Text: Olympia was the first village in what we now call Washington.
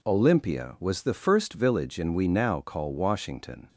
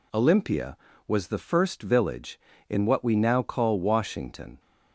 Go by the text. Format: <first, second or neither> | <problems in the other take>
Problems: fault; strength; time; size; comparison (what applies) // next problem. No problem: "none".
second | skips "what"; at 2.1 s